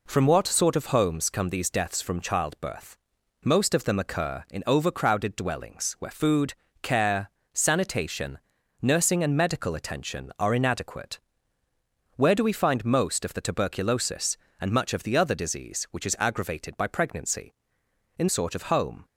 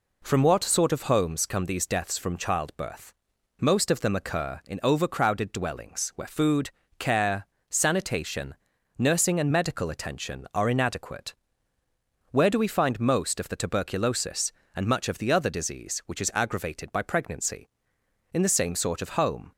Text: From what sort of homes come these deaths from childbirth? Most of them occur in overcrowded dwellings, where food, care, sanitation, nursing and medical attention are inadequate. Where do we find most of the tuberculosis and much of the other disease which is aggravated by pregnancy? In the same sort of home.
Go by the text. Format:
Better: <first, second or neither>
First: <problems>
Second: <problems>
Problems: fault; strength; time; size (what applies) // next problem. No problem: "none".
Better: second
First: skips "the same"; at 18.2 s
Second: none